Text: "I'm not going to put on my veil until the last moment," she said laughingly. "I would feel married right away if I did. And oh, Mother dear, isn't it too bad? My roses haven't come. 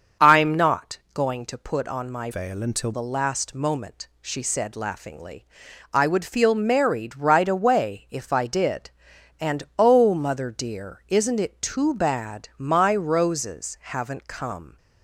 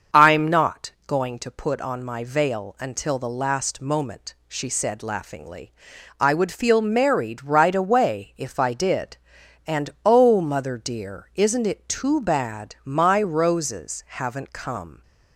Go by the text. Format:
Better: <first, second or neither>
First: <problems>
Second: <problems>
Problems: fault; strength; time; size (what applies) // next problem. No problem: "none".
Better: second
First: starts louder than the rest; until 1.3 s; 7 dB // pauses between "not" and "going"; slight; at 0.9 s; 0.16 s long // changes voice from "veil" to "until"; from 2.3 to 2.9 s; 0.6 s long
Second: starts louder than the rest; until 1.3 s; 6.5 dB // pauses between "not" and "going"; slight; at 0.8 s; 0.16 s long